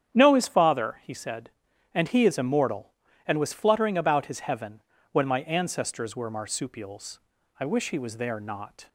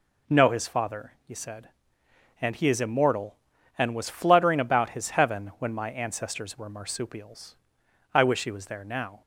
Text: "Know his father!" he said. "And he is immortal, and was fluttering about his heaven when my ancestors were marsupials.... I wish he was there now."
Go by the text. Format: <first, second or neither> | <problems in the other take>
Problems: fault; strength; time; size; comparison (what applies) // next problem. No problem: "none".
second | starts louder than the rest; strong; until 1.1 s; 9 dB // pauses between "heaven" and "when"; slight; at 4.8 s; 0.30 s long // says "not" for "now"; at 8.3 s